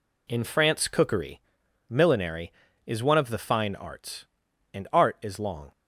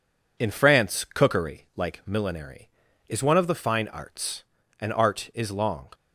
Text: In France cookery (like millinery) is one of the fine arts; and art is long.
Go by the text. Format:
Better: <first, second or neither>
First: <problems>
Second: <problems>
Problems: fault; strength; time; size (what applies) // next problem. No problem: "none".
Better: second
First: skips "like"; at 1.6 s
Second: none